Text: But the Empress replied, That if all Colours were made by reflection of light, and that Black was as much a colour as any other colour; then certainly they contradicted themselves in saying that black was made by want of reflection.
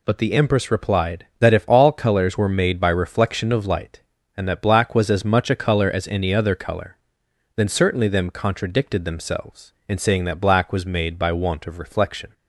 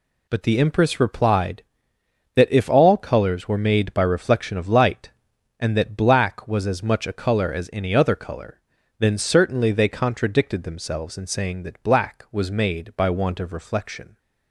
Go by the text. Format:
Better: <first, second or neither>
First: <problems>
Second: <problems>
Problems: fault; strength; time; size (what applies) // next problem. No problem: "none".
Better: second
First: says "them" for "they"; at 8.0 s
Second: none